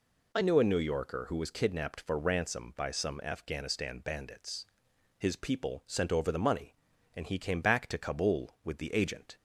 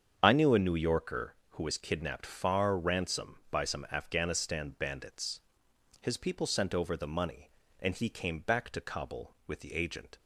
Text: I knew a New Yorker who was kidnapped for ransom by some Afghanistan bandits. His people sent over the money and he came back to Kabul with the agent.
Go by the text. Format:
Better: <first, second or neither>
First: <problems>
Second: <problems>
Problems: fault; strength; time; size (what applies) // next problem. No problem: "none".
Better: first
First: none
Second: starts louder than the rest; strong; until 1.2 s; 7.5 dB // says "far" for "for"; at 2.2 s